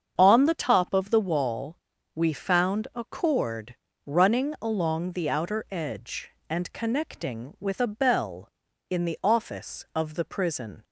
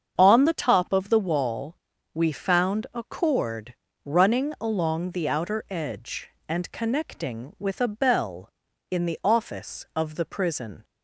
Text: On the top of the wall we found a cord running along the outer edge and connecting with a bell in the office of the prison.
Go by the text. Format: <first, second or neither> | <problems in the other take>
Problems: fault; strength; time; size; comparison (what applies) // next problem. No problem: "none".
neither | starts louder than the rest; strong; the same in both // pauses between "wall" and "we"; the same in both // pauses between "cord" and "running"; slight; the same in both